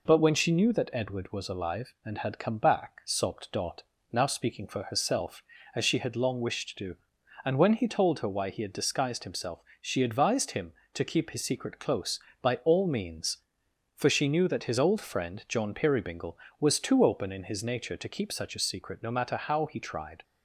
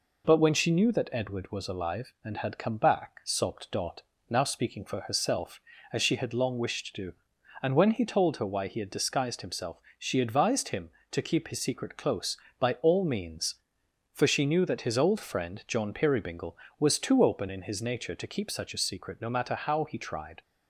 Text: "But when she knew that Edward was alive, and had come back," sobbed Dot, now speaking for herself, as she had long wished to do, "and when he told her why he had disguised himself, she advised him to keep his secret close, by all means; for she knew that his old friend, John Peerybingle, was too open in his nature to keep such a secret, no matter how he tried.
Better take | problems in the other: neither | none

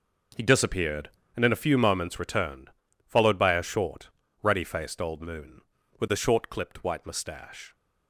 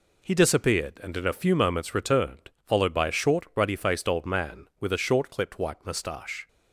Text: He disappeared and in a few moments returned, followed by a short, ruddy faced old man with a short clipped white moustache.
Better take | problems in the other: second | says "moon" for "man"; at 5.2 s

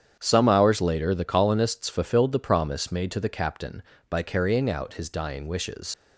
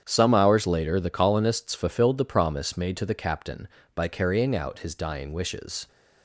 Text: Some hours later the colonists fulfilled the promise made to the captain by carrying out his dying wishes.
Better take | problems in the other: second | starts louder than the rest; strong; until 1.2 s; 8.5 dB; strong in the second // leaves "wishes" unfinished; at 5.9 s; 80 ms

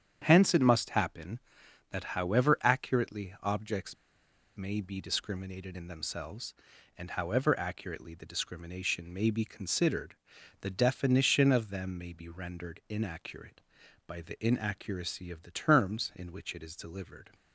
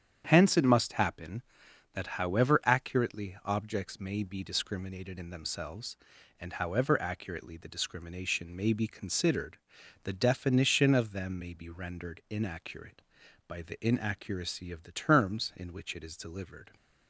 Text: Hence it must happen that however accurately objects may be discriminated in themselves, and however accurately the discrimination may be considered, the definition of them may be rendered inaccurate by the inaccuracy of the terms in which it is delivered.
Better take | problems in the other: second | starts louder than the rest; strong; until 1.2 s; 8.5 dB; strong in the second // pauses between "objects" and "may"; noticeable; at 3.9 s; 0.62 s long

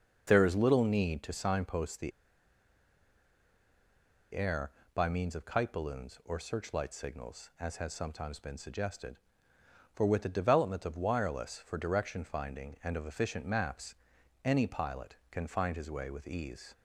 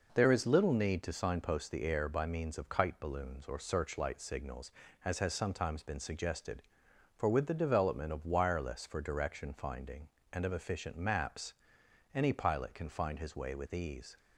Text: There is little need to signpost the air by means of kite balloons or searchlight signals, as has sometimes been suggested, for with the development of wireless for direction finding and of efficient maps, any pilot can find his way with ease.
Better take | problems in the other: second | starts louder than the rest; until 1.2 s; 6.5 dB // pauses between "the" and "air"; strong; at 2.1 s; 2.2 s long

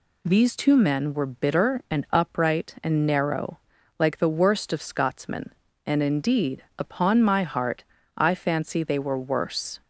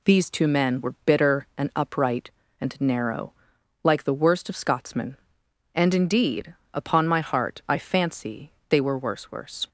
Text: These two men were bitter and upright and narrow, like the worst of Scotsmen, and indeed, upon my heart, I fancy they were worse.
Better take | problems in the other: first | pauses between "fancy" and "they"; slight; at 8.5 s; 0.16 s long // says "worse" twice; at 9.3 s

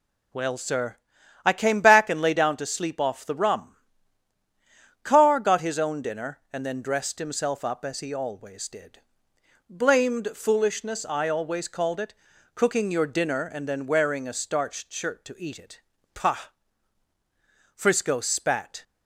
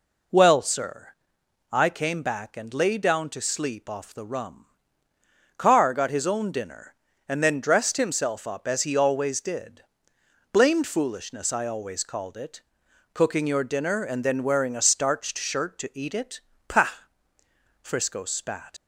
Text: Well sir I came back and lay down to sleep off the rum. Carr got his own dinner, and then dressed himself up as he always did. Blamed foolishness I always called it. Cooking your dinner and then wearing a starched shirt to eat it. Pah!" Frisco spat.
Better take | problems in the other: first | pauses between "sir" and "I"; noticeable; at 1.0 s; 0.64 s long; noticeable in the first // leaves "spat" unfinished; at 18.7 s; 55 ms

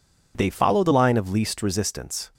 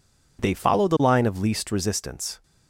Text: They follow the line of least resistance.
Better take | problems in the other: neither | none

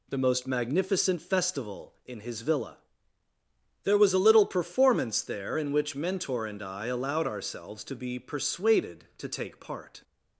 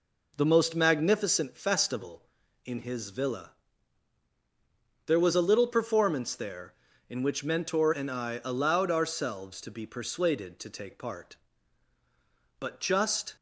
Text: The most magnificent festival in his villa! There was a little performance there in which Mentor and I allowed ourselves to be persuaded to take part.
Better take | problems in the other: first | goes on to say "But just"; noticeable; from 12.5 s on; 0.76 s long

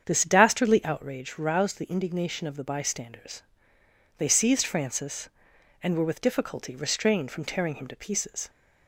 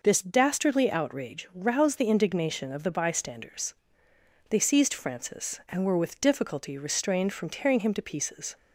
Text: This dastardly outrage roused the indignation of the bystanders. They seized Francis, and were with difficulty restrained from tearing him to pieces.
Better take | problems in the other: second | starts louder than the rest; strong; until 1.2 s; 8 dB

